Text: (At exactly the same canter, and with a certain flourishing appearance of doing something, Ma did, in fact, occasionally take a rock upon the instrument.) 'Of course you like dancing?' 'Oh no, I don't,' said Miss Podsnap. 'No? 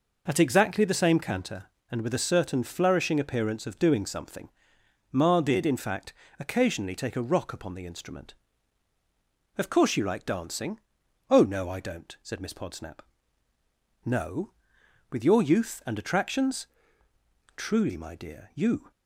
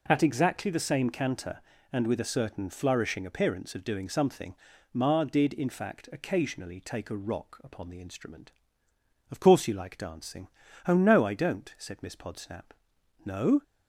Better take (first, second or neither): second